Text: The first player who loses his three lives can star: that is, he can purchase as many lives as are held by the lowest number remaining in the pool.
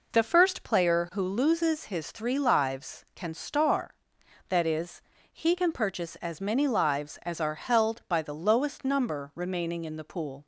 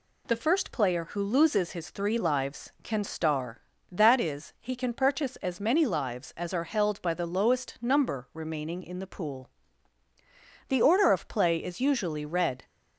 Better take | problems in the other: first | goes on to say "The order of play is usually red"; strong; from 10.6 s on; 1.9 s long

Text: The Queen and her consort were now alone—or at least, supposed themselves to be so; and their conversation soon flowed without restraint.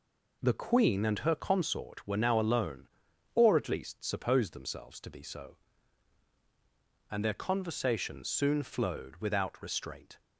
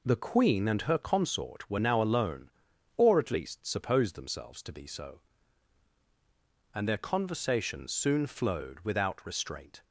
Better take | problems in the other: neither | none

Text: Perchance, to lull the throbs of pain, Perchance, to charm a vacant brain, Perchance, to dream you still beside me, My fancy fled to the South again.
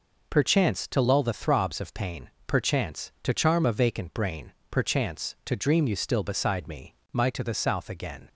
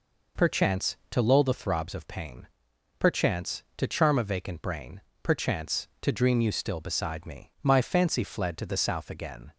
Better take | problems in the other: second | skips "fancy fled"; at 7.2 s

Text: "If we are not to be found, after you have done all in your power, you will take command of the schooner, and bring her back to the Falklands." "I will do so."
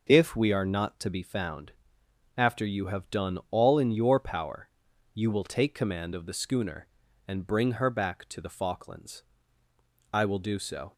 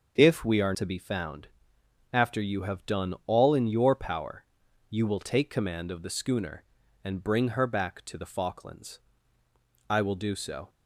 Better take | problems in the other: first | starts louder than the rest; until 1.2 s; 6.5 dB // skips "not"; at 0.7 s

